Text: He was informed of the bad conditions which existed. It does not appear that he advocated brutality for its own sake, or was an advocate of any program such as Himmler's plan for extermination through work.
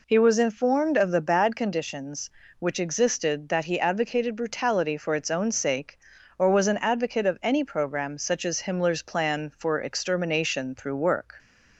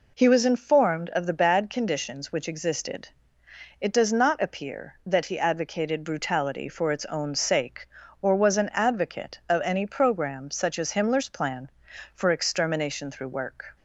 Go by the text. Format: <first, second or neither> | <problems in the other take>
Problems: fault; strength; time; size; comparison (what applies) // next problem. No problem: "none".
second | skips "It does not appear"; at 3.4 s